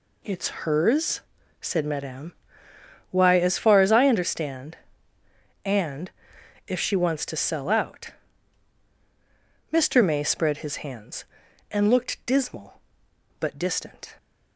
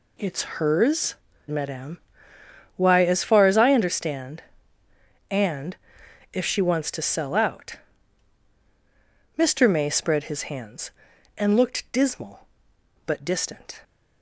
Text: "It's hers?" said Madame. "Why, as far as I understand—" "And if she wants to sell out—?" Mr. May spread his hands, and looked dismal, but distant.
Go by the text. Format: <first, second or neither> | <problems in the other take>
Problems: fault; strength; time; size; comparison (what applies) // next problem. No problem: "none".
first | pauses between "It's" and "hers"; slight; at 0.4 s; 0.16 s long; slight in the first // skips "said"; at 1.3 s // pauses between "And" and "if"; noticeable; at 5.7 s; 0.54 s long; noticeable in the first